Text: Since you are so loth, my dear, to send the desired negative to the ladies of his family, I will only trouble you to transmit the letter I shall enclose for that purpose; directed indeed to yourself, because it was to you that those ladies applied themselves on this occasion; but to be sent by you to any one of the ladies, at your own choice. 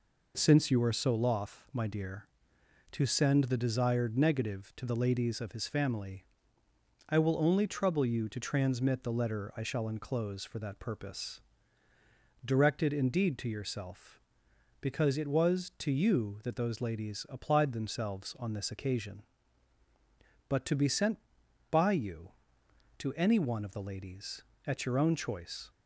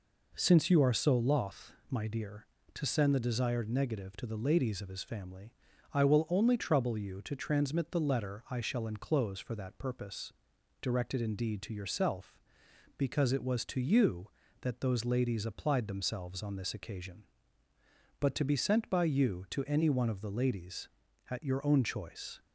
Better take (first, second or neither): neither